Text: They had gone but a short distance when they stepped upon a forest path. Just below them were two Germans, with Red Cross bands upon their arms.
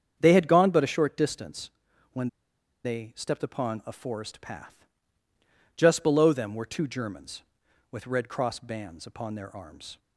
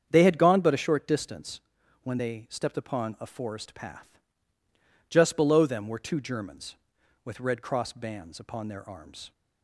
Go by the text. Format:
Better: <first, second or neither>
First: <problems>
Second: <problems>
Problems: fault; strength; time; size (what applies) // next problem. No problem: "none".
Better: second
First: starts louder than the rest; strong; until 1.2 s; 8 dB // pauses between "distance" and "when"; at 1.6 s; 0.44 s long // pauses between "when" and "they"; noticeable; at 2.2 s; 0.57 s long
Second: starts louder than the rest; strong; until 1.1 s; 8 dB // pauses between "distance" and "when"; at 1.5 s; 0.44 s long